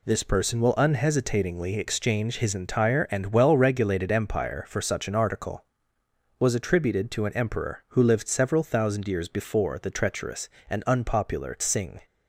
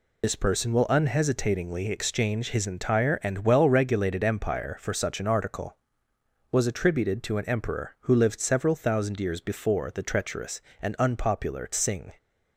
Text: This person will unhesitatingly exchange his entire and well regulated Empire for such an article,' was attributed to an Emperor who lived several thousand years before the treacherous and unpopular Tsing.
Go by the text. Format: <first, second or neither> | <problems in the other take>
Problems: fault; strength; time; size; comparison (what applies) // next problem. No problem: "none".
first | loses the start of "This"; at 0.2 s; 65 ms